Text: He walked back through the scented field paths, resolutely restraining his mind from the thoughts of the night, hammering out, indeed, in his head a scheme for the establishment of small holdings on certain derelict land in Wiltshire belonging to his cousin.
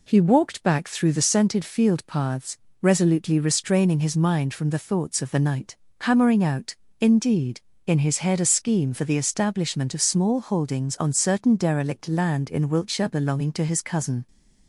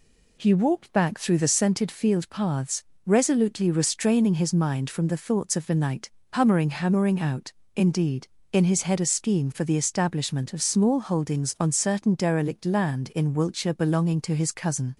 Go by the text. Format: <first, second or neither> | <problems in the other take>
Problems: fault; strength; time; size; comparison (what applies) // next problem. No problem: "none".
first | says "hammering" twice; at 6.6 s